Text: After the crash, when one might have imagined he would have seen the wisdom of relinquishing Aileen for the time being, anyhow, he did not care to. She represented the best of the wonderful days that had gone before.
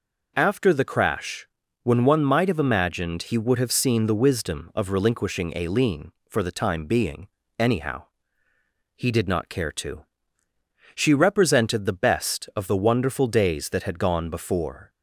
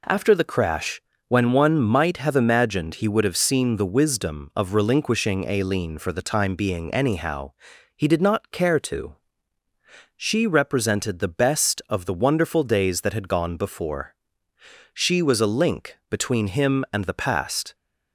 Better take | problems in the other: first | goes on to say "She was a link between him and the past"; strong; from 14.9 s on; 2.8 s long

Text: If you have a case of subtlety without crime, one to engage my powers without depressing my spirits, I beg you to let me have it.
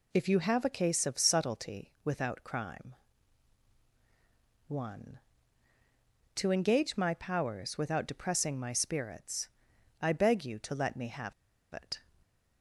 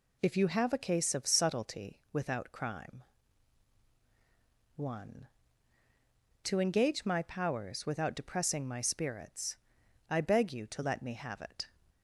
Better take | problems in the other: second | pauses between "have" and "it"; at 11.3 s; 0.41 s long // stays silent after the last word; slight; from 11.9 s on; 0.7 s long

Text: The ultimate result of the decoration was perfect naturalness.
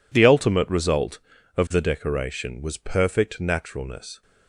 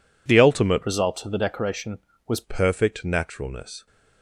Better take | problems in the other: first | changes voice from "result" to "was"; from 0.8 to 2.4 s; 1.6 s long

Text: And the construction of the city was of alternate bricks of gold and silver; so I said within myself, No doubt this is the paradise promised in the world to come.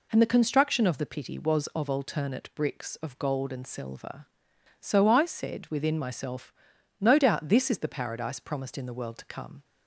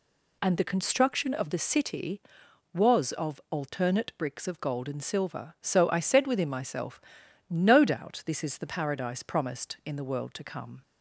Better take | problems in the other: second | says "pity" for "city"; at 1.0 s

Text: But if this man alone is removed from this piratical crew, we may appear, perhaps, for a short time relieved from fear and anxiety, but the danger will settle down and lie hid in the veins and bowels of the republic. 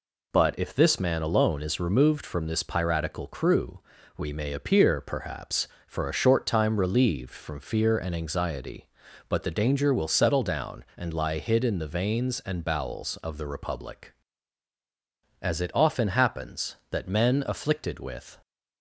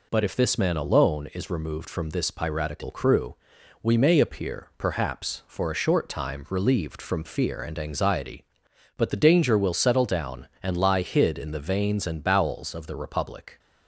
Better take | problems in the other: second | goes on to say "As it often happens that men afflicted with"; strong; from 15.4 s on; 3.0 s long

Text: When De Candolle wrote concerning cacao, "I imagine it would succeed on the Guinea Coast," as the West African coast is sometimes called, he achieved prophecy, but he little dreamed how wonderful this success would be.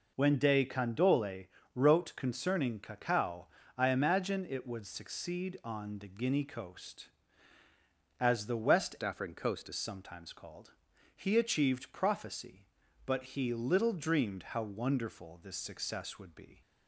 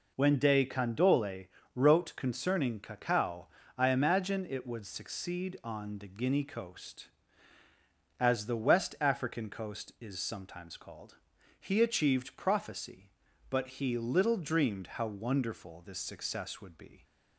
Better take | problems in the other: second | pauses between "Candolle" and "wrote"; slight; at 1.4 s; 0.28 s long; slight in the second // changes voice from "African" to "is"; from 9.0 to 9.7 s; 0.7 s long

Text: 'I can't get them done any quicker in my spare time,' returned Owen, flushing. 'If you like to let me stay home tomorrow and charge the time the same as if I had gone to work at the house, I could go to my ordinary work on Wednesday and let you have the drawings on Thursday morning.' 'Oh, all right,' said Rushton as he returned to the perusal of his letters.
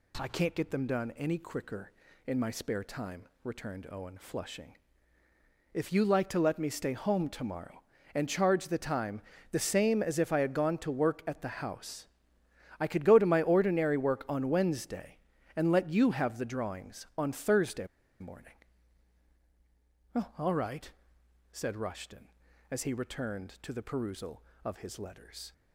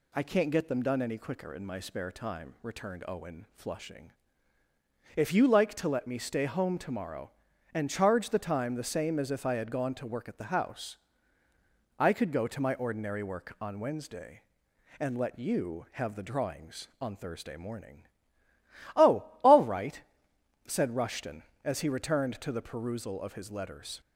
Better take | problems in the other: second | pauses between "time" and "the"; slight; at 9.2 s; 0.30 s long // pauses between "Thursday" and "morning"; slight; at 17.8 s; 0.34 s long

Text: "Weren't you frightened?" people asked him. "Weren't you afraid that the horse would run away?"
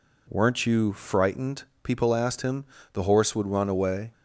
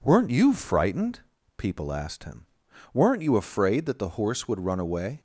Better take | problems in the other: second | skips "Weren't you afraid that"; at 2.7 s

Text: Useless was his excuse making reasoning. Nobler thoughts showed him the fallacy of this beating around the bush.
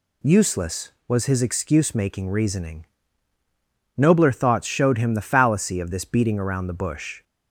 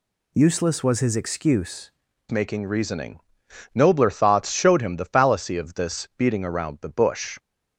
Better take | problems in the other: first | changes voice at "making"; from 2.2 s on; 5.1 s long

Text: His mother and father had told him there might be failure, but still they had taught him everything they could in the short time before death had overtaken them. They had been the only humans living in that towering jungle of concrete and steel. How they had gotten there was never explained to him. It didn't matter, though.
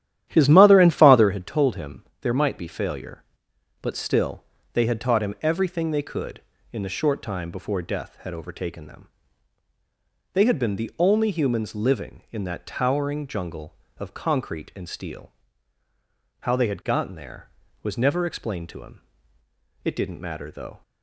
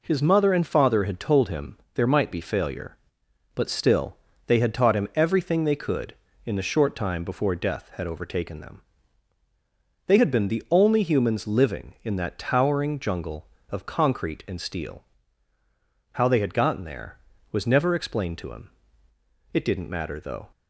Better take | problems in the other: second | starts louder than the rest; strong; until 1.3 s; 11.5 dB // pauses between "him" and "there"; slight; at 2.0 s; 0.16 s long; slight in the second // pauses between "still" and "they"; slight; at 4.4 s; 0.30 s long; slight in the second

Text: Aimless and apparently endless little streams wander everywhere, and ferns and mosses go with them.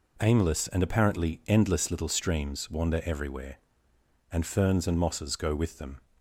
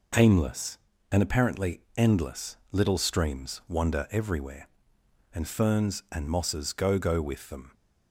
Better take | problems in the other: first | pauses between "apparently" and "endless"; slight; at 1.7 s; 0.18 s long // pauses between "endless" and "little"; slight; at 2.5 s; 0.16 s long // says "go" twice; at 6.9 s

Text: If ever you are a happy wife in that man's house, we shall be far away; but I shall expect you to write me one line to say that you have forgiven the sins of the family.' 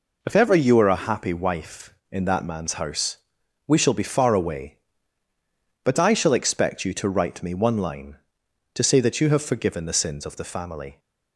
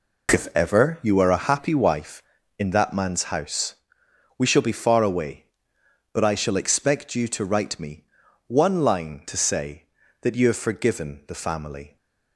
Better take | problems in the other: first | pauses between "me" and "one"; at 8.0 s; 0.42 s long // skips "the sins of"; at 11.2 s

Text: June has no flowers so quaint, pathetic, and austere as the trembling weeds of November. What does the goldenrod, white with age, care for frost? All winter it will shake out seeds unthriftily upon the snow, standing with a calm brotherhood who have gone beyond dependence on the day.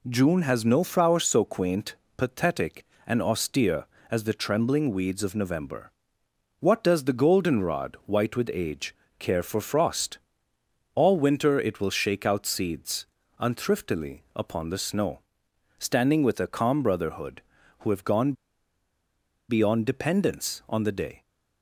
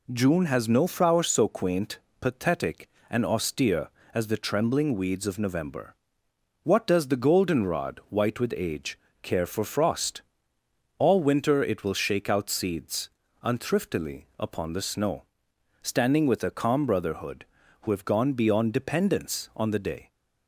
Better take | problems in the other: second | pauses between "seeds" and "unthriftily"; slight; at 13.0 s; 0.34 s long; slight in the second // pauses between "gone" and "beyond"; at 18.3 s; 1.1 s long

